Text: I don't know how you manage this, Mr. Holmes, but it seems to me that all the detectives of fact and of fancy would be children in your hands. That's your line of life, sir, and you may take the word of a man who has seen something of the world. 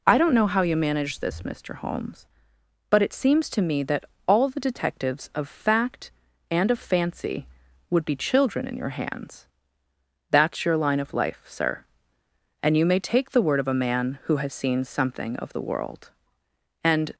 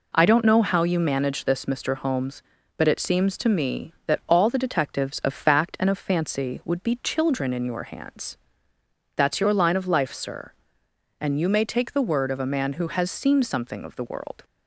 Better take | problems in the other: second | pauses between "that" and "all"; slight; at 4.0 s; 0.22 s long // goes on to say "And"; slight; from 16.8 s on; 0.32 s long

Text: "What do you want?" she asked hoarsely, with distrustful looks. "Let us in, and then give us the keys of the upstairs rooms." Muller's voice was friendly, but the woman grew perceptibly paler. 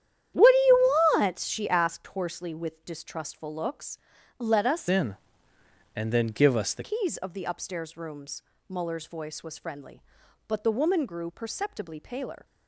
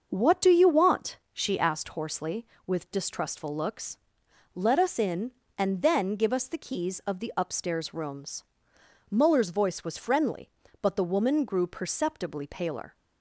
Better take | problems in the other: second | starts louder than the rest; strong; until 1.5 s; 9.5 dB; also in the second // pauses between "you" and "want"; slight; at 0.9 s; 0.22 s long // changes voice from "in" to "the"; from 4.8 to 6.8 s; 2.0 s long

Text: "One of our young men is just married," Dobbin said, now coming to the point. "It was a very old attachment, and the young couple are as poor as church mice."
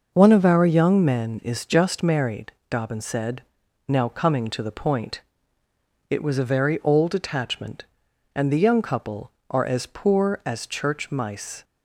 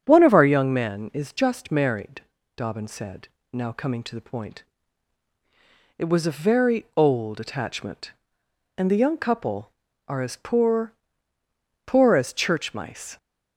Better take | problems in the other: first | starts louder than the rest; strong; until 1.0 s; 7.5 dB // says "poor" twice; at 11.8 s

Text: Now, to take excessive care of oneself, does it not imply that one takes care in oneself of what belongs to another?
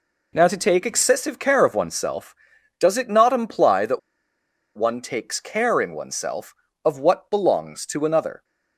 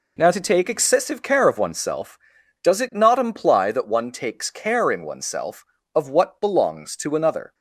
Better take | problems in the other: second | pauses between "that" and "one"; noticeable; at 3.9 s; 0.77 s long

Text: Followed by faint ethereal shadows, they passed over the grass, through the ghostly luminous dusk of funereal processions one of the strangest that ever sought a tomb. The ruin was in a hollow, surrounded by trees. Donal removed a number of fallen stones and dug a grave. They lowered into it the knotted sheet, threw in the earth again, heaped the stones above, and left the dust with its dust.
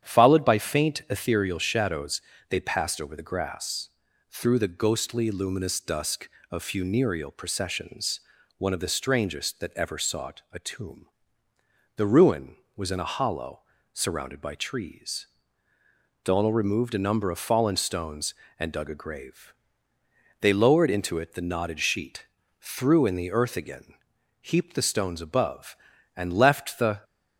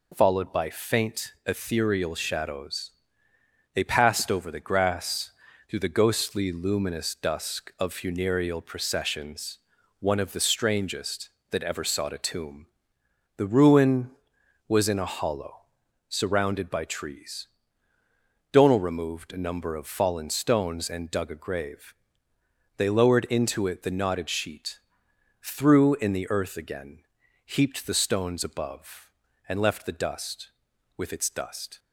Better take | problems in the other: second | starts louder than the rest; strong; until 1.1 s; 9 dB // pauses between "processions" and "one"; at 8.1 s; 0.38 s long; also in the second // stops before "dust with its dust"; at 27.0 s

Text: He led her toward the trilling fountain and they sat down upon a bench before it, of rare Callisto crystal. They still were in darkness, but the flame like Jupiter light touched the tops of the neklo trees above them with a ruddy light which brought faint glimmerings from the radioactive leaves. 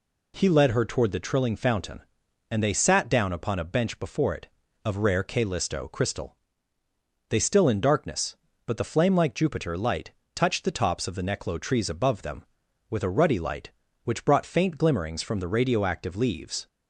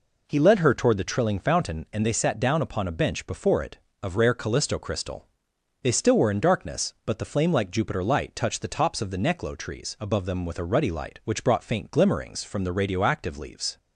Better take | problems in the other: second | skips "were"; at 7.6 s // pauses between "light" and "touched"; slight; at 10.1 s; 0.24 s long

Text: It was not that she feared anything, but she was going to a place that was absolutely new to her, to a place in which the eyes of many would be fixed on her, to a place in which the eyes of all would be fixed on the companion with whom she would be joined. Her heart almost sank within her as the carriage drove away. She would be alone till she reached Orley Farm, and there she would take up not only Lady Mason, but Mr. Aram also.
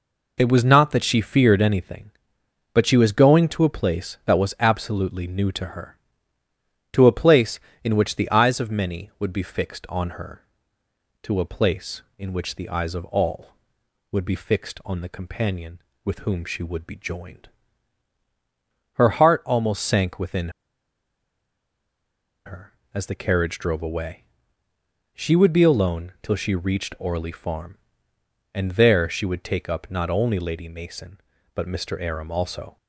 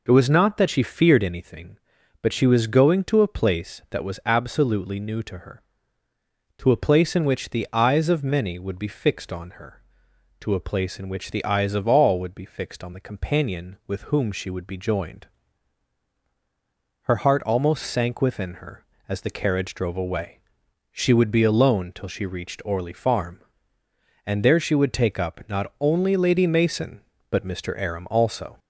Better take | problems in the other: second | pauses between "within" and "her"; strong; at 20.4 s; 1.9 s long

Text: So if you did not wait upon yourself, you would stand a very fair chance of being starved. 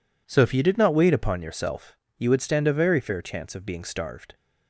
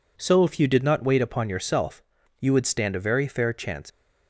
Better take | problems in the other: first | stops before "of being starved"; at 3.9 s

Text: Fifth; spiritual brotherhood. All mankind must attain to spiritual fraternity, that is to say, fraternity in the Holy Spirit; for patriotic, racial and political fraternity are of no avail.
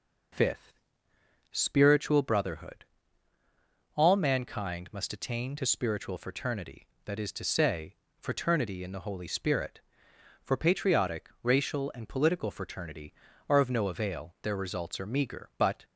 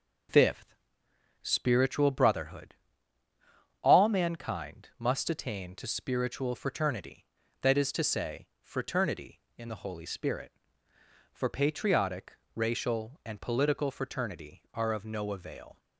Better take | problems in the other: second | goes on to say "Their results are meager but"; from 14.4 s on; 1.4 s long

